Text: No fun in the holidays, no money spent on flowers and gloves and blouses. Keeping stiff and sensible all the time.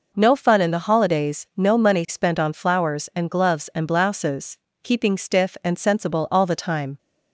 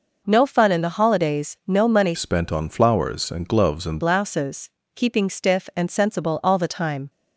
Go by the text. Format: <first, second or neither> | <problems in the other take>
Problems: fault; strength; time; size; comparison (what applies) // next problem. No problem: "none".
first | changes voice from "spent" to "and"; from 2.1 to 4.0 s; 1.9 s long